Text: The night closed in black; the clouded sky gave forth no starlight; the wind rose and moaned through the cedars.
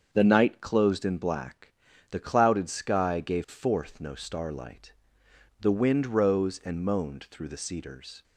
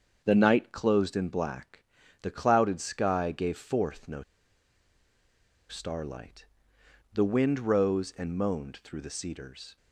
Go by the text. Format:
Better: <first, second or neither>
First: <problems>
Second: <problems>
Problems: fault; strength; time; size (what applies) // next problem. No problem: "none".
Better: first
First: starts louder than the rest; until 1.1 s; 7 dB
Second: starts louder than the rest; until 1.2 s; 7 dB // pauses between "no" and "starlight"; strong; at 4.2 s; 1.4 s long